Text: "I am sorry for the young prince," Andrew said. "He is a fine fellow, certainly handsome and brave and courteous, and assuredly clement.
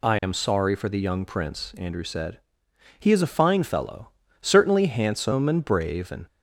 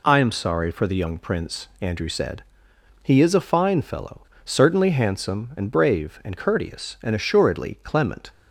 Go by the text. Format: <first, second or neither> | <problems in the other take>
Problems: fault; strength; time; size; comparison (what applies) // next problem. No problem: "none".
second | stops before "courteous and assuredly clement"; at 6.2 s